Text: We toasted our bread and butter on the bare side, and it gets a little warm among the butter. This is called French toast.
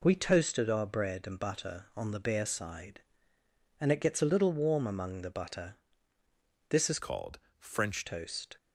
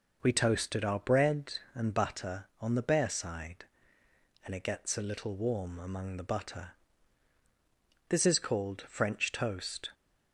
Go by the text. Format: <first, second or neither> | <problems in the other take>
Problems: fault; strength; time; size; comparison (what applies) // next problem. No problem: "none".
second | changes voice from "called" to "French"; from 6.9 to 8.0 s; 1.1 s long // pauses between "called" and "French"; slight; at 7.3 s; 0.20 s long